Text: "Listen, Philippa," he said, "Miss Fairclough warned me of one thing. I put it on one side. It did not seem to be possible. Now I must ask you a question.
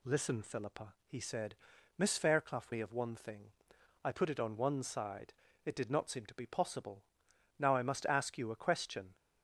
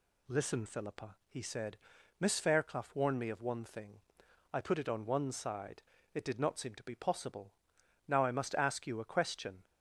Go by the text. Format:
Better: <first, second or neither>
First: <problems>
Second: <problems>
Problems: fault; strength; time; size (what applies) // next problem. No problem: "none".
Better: second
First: skips "warned"; at 2.7 s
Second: none